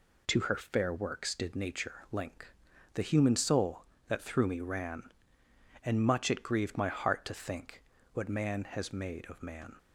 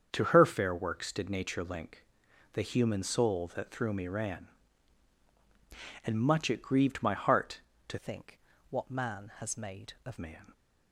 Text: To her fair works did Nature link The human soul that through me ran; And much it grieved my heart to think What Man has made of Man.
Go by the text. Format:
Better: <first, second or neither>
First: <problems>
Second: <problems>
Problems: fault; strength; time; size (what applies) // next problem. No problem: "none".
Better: first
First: pauses between "link" and "The"; at 2.5 s; 0.40 s long // pauses between "think" and "What"; slight; at 7.8 s; 0.30 s long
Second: starts louder than the rest; strong; until 1.1 s; 7 dB // pauses between "link" and "The"; noticeable; at 2.0 s; 0.48 s long // changes voice from "think" to "of"; from 7.9 to 10.1 s; 2.2 s long // pauses between "think" and "What"; slight; at 8.3 s; 0.30 s long